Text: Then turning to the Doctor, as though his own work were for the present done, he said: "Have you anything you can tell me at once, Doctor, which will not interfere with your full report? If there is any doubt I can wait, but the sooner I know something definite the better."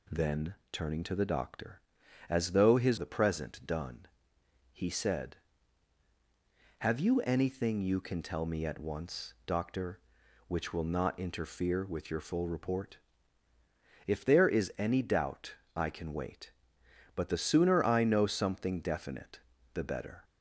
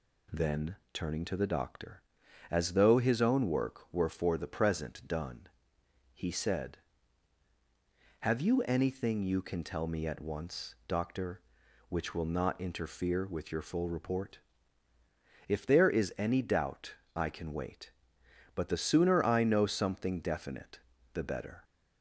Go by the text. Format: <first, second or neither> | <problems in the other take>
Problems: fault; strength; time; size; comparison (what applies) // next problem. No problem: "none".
second | pauses between "Then" and "turning"; slight; at 0.5 s; 0.18 s long; slight in the second // skips "own work were for"; at 2.9 s // pauses between "doubt" and "I"; slight; at 15.5 s; 0.20 s long; slight in the second // pauses between "definite" and "the"; slight; at 19.3 s; 0.34 s long; slight in the second